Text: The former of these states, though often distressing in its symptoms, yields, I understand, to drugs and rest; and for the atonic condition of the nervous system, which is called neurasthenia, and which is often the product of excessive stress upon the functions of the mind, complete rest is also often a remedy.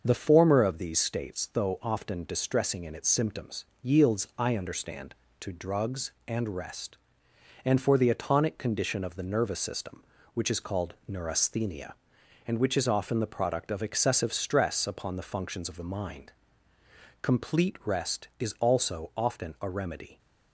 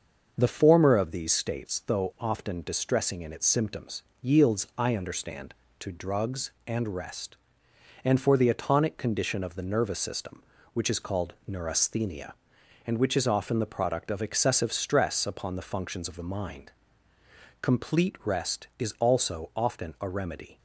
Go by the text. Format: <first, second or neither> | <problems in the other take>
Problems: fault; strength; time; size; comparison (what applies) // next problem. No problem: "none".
neither | starts louder than the rest; the same in both // pauses between "called" and "neurasthenia"; slight; the same in both